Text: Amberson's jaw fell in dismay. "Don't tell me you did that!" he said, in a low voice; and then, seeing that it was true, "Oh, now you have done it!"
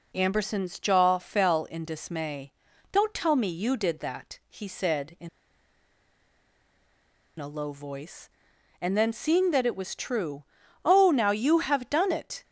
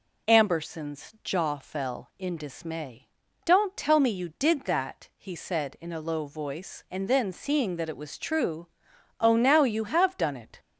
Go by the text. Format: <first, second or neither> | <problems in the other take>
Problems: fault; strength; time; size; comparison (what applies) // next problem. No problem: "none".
second | pauses between "in" and "a"; strong; at 5.2 s; 2.1 s long